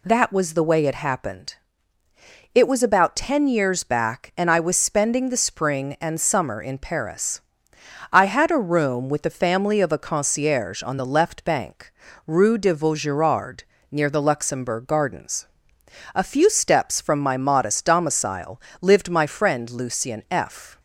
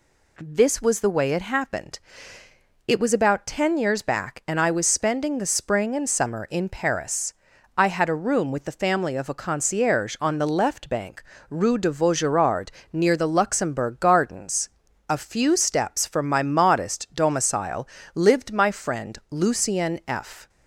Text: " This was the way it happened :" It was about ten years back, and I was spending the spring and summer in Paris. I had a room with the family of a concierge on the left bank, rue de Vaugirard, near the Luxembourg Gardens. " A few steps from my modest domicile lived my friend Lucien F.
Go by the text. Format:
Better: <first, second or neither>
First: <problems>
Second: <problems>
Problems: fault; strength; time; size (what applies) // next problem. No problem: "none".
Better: second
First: says "That" for "This"; at 0.0 s // pauses between "domicile" and "lived"; slight; at 18.5 s; 0.22 s long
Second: pauses between "domicile" and "lived"; slight; at 17.8 s; 0.24 s long